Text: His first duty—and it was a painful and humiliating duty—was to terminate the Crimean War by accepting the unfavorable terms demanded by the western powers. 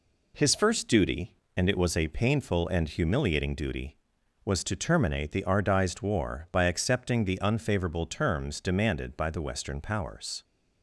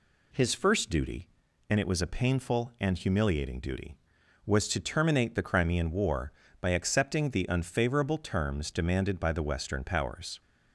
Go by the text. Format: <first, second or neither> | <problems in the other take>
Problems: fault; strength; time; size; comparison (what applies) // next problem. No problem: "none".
second | says "Ardized" for "Crimean"; at 5.4 s